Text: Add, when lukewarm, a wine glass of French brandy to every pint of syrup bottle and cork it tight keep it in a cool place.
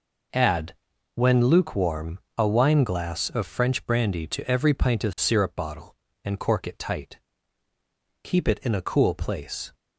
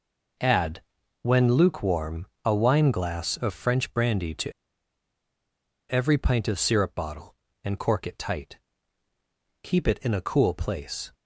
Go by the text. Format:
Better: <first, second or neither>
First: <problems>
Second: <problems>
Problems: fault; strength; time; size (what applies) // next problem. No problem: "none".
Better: first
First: pauses between "tight" and "keep"; at 7.1 s; 1.0 s long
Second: pauses between "to" and "every"; strong; at 4.5 s; 1.3 s long // pauses between "tight" and "keep"; at 8.5 s; 1.0 s long